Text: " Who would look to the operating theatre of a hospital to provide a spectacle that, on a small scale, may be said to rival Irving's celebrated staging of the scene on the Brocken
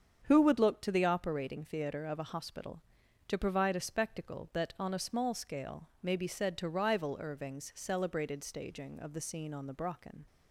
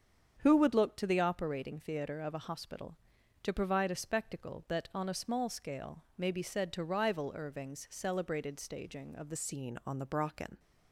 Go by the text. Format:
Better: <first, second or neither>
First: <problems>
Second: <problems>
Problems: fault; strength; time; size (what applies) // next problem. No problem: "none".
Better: first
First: starts louder than the rest; strong; until 1.2 s; 7.5 dB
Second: starts louder than the rest; strong; until 1.4 s; 7.5 dB // changes voice at "scene"; from 9.3 s on; 1.2 s long